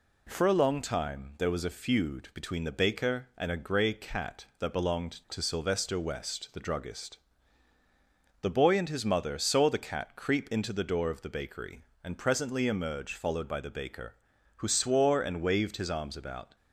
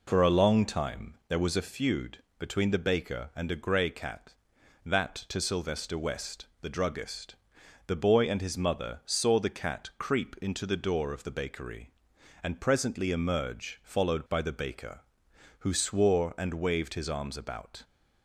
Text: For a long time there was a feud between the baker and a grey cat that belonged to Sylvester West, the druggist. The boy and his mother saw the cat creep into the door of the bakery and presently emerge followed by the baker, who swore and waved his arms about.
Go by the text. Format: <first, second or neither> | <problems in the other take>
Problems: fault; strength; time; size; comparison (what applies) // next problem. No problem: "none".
first | pauses between "feud" and "between"; slight; at 2.2 s; 0.16 s long // skips "belonged"; at 5.2 s